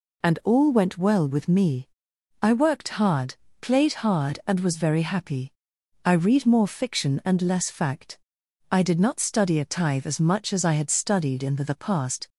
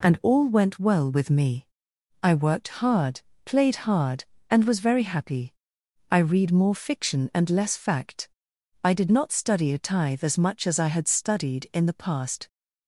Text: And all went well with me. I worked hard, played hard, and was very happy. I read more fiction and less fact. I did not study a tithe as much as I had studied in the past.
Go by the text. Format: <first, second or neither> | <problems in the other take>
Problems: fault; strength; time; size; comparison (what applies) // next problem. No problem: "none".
second | says "the" twice; at 11.6 s